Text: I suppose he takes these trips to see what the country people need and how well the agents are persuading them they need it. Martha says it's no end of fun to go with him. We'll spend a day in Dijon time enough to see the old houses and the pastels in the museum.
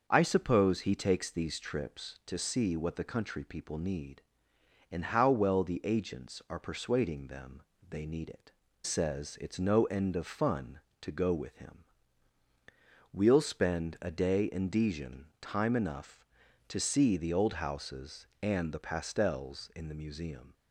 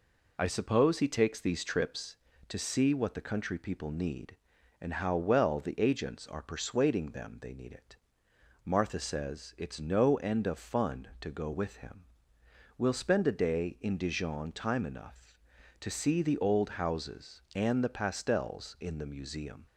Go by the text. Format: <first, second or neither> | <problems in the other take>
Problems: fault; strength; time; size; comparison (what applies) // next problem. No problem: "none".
second | starts louder than the rest; until 1.0 s; 6 dB // pauses between "them" and "they"; slight; at 7.6 s; 0.26 s long // skips "Martha"; at 8.6 s